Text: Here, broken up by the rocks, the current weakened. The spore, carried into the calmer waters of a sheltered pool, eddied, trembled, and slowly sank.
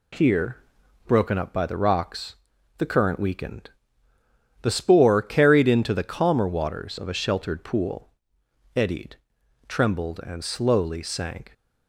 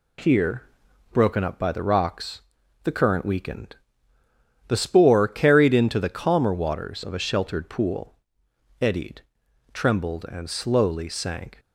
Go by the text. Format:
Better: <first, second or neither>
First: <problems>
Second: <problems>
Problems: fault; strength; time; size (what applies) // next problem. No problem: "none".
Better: neither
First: none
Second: none